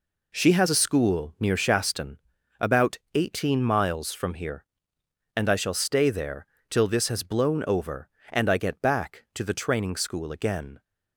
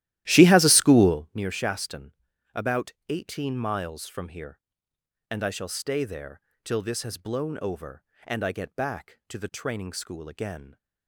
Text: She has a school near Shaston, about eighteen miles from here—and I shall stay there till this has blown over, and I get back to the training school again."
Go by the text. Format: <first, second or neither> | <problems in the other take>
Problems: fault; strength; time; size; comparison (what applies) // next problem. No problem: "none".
first | starts louder than the rest; strong; until 1.3 s; 14.5 dB // pauses between "about" and "eighteen"; slight; at 2.9 s; 0.16 s long; slight in the first // pauses between "there" and "till"; slight; at 6.4 s; 0.22 s long; slight in the first